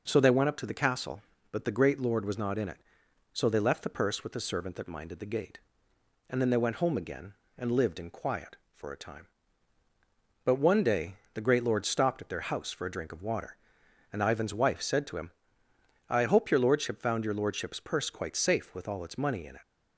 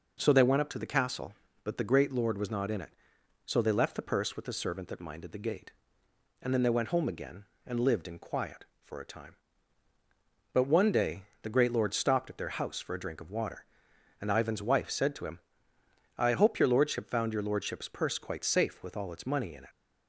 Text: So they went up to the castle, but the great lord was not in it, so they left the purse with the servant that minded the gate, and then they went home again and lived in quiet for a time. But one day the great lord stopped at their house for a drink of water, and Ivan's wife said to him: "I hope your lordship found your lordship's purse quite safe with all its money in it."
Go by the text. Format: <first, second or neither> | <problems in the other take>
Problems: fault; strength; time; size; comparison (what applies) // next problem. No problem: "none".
neither | pauses between "day" and "the"; slight; the same in both